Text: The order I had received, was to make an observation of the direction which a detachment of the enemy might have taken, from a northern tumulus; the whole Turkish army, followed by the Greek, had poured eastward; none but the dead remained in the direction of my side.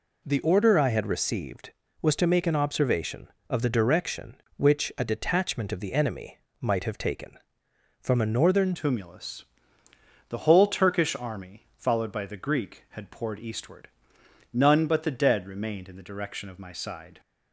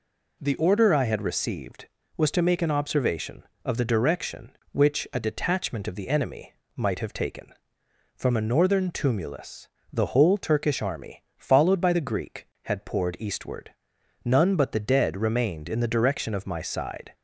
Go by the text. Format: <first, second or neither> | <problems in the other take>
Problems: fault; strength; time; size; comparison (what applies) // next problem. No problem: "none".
second | pauses between "enemy" and "might"; slight; at 6.3 s; 0.24 s long; slight in the second // changes voice at "tumulus"; from 8.7 s on; 8.4 s long